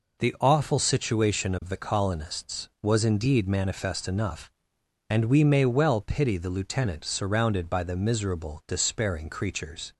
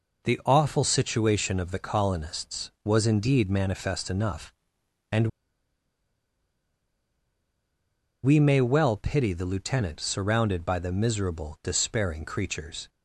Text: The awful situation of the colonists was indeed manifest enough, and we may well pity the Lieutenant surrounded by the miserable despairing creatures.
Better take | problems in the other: first | pauses between "and" and "we"; strong; at 5.2 s; 2.9 s long

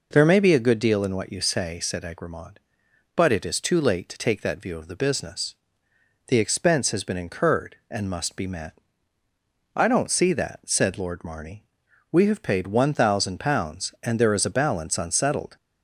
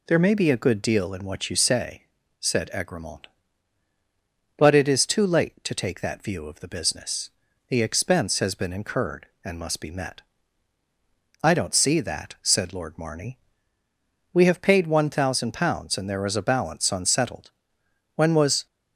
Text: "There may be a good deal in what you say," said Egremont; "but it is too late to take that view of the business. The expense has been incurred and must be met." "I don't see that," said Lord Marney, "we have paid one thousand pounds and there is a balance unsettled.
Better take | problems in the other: first | goes on to say "When was"; from 18.1 s on; 0.52 s long

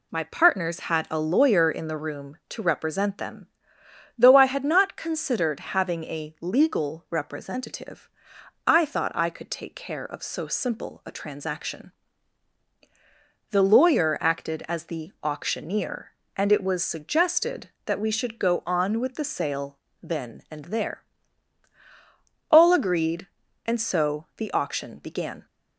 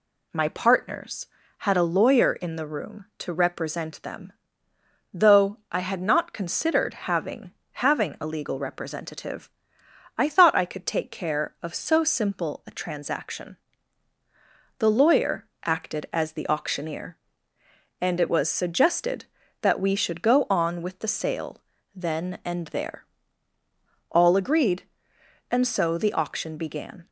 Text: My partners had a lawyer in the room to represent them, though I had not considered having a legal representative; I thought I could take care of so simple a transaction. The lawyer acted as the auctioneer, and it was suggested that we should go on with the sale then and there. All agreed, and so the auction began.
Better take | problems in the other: first | says "having" twice; at 7.7 s // pauses between "lawyer" and "acted"; slight; at 15.4 s; 0.18 s long // pauses between "sale" and "then"; slight; at 21.6 s; 0.32 s long; slight in the first

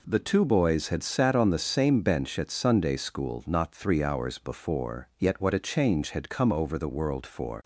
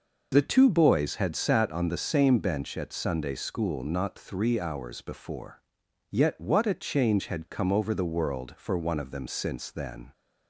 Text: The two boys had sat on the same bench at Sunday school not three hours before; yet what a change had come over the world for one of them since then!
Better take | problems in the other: second | stops before "one of them since then"; at 7.6 s

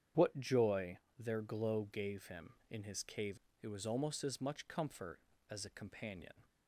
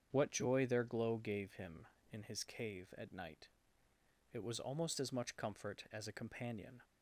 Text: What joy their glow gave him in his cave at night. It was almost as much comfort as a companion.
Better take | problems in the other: second | starts louder than the rest; strong; until 1.3 s; 8.5 dB; strong in the second // pauses between "joy" and "their"; slight; at 0.9 s; 0.22 s long // skips "at night"; at 3.4 s

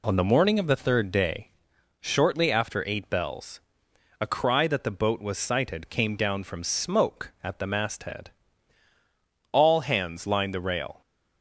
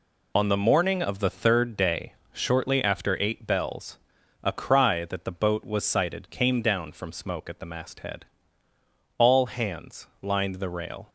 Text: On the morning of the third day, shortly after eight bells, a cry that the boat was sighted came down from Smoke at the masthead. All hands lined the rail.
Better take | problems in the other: neither | none

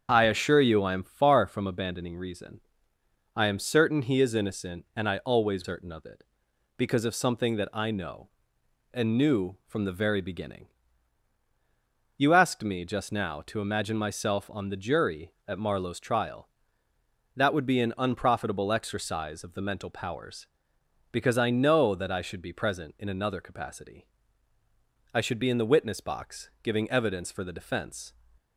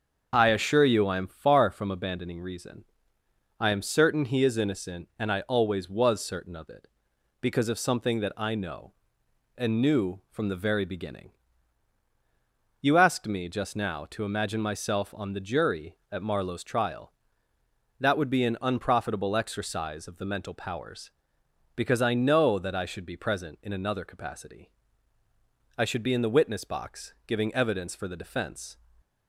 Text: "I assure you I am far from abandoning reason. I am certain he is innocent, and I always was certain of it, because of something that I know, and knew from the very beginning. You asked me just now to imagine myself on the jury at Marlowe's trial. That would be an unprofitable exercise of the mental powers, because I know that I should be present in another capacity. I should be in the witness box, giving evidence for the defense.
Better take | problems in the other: second | starts louder than the rest; strong; until 1.1 s; 7.5 dB; also in the second // skips "was"; at 5.6 s

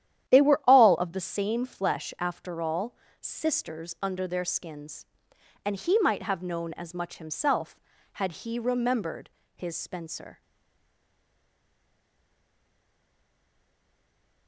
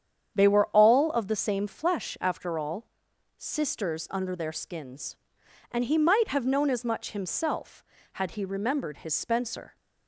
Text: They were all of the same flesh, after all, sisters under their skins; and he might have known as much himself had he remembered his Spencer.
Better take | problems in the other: second | starts louder than the rest; strong; until 1.3 s; 11 dB; strong in the second // pauses between "remembered" and "his"; slight; at 9.2 s; 0.26 s long // stays silent after the last word; strong; from 10.4 s on; 4.0 s long

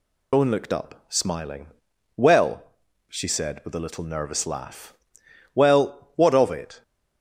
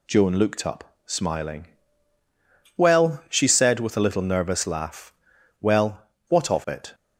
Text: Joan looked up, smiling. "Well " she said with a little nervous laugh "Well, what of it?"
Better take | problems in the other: second | loses the start of "Joan"; at 0.3 s; 135 ms // pauses between "laugh" and "Well"; noticeable; at 4.9 s; 0.60 s long; noticeable in the second

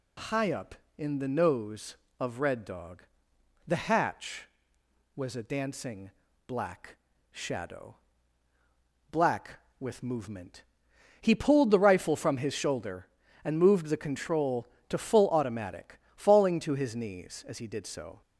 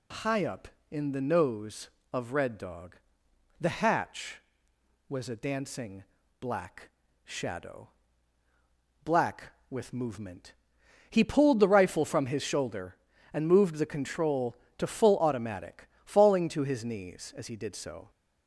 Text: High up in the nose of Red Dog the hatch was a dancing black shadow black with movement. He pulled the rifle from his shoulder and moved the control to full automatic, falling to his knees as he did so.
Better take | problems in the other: neither | pauses between "Dog" and "the"; noticeable; the same in both // pauses between "dancing" and "black"; slight; the same in both // pauses between "black" and "shadow"; slight; the same in both // pauses between "shadow" and "black"; the same in both

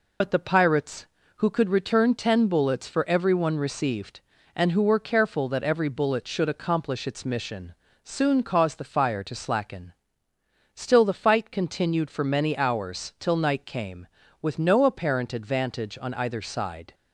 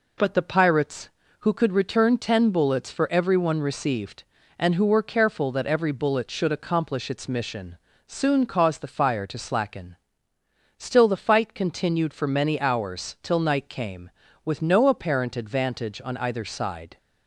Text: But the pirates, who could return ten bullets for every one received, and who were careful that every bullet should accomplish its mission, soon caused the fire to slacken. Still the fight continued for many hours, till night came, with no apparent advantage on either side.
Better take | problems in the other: second | loses the start of "But"; at 0.2 s; 55 ms

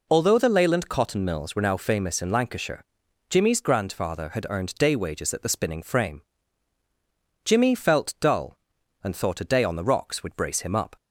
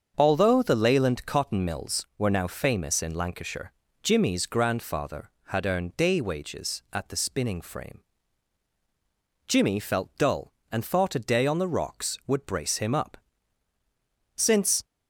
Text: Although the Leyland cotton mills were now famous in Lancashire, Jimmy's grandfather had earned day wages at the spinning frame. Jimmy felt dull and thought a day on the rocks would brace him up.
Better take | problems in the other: first | starts louder than the rest; until 1.1 s; 6.5 dB // goes on to say "Since"; slight; from 14.3 s on; 0.48 s long

